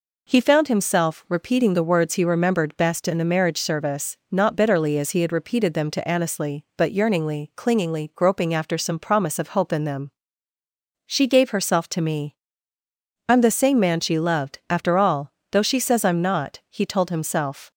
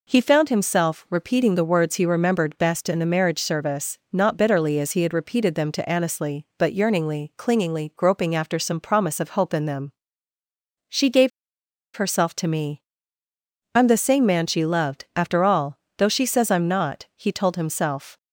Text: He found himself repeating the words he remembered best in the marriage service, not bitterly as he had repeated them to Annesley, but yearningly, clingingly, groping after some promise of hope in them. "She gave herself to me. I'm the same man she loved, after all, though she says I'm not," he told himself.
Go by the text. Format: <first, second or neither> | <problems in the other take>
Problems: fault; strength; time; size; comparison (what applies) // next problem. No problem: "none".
first | pauses between "gave" and "herself"; noticeable; at 11.3 s; 0.66 s long